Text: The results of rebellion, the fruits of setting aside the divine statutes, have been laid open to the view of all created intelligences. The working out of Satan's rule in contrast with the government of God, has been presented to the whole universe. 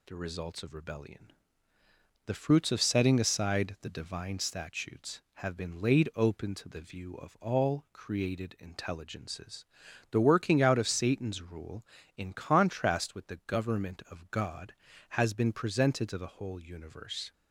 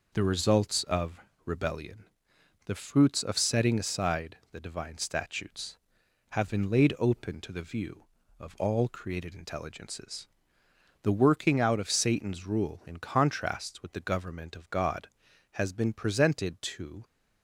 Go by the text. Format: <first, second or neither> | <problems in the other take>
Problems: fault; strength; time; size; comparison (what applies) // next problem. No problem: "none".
first | pauses between "of" and "rebellion"; slight; at 1.2 s; 0.26 s long // stops before "the whole universe"; at 17.0 s